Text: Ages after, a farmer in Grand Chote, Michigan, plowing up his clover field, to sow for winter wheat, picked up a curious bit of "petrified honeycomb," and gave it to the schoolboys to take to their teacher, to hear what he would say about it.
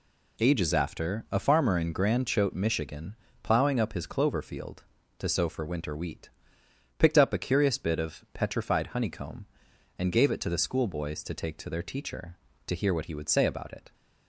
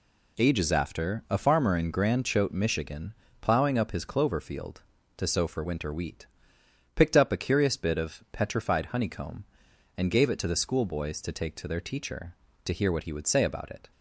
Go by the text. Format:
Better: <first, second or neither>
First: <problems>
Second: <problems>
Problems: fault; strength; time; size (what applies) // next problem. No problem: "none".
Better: neither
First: none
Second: none